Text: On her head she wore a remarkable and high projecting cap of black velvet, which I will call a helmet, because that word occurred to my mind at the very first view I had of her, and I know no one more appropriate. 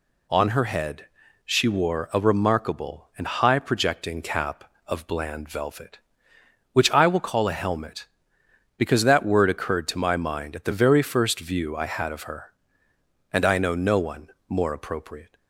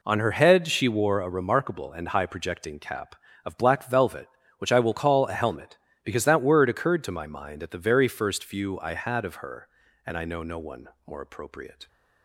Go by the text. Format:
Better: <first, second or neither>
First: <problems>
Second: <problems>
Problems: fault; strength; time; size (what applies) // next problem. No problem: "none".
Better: second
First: pauses between "head" and "she"; at 1.0 s; 0.40 s long // says "bland" for "black"; at 5.0 s // pauses between "one" and "more"; slight; at 14.2 s; 0.22 s long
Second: pauses between "one" and "more"; slight; at 10.8 s; 0.18 s long